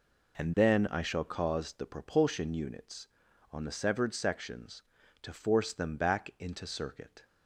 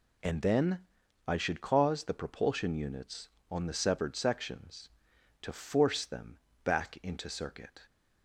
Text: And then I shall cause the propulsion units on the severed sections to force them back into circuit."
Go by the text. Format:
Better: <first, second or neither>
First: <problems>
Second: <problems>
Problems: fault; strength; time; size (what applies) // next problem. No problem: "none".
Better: first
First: none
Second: pauses between "then" and "I"; noticeable; at 0.7 s; 0.48 s long // says "should" for "shall"; at 1.3 s // pauses between "them" and "back"; slight; at 6.3 s; 0.26 s long